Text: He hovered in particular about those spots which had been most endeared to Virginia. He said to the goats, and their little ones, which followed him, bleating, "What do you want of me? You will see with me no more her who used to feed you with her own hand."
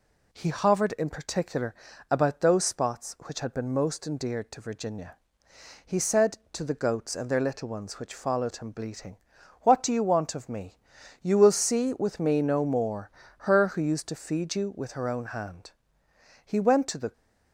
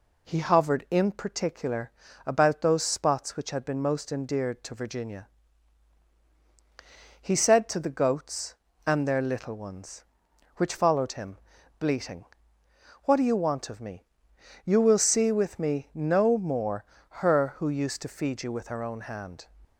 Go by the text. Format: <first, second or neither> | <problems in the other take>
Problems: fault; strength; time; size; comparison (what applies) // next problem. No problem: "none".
second | pauses between "particular" and "about"; slight; at 1.7 s; 0.36 s long; slight in the second // pauses between "more" and "her"; slight; at 13.1 s; 0.30 s long; slight in the second // goes on to say "He went to the"; noticeable; from 16.4 s on; 0.66 s long